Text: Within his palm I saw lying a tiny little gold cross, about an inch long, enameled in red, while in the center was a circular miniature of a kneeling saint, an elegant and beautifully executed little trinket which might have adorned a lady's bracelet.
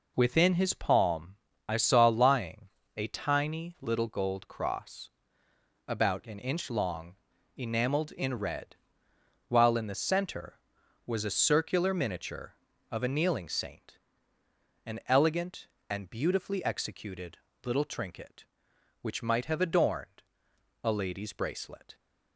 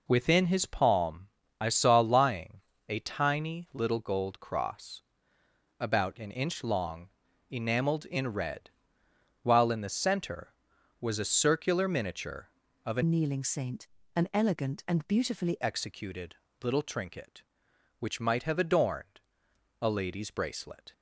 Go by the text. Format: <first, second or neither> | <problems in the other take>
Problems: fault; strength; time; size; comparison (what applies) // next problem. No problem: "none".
first | pauses between "palm" and "I"; slight; at 1.2 s; 0.32 s long; slight in the first // pauses between "lying" and "a"; slight; at 2.6 s; 0.26 s long; slight in the first // changes voice from "kneeling" to "beautifully"; from 13.0 to 15.5 s; 2.5 s long // pauses between "executed" and "little"; slight; at 16.3 s; 0.26 s long; slight in the first // pauses between "adorned" and "a"; noticeable; at 19.1 s; 0.62 s long; noticeable in the first